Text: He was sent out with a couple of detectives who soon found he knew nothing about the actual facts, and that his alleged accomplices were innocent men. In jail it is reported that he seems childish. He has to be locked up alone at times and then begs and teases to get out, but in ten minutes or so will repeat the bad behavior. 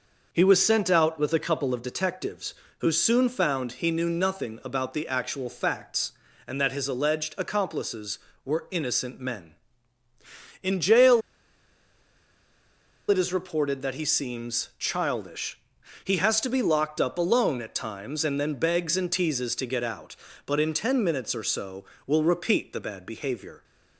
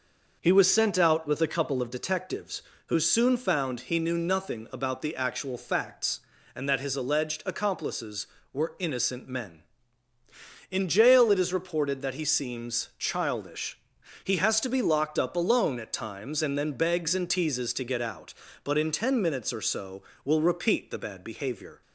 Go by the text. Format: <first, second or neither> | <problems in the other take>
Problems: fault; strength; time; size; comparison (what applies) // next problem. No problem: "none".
second | pauses between "jail" and "it"; strong; at 11.2 s; 1.8 s long